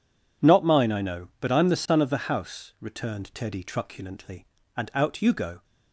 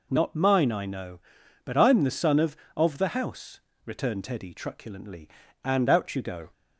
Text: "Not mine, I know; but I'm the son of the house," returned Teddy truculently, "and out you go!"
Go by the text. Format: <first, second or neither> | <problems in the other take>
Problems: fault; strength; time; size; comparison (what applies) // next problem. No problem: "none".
first | says "of" twice; at 2.7 s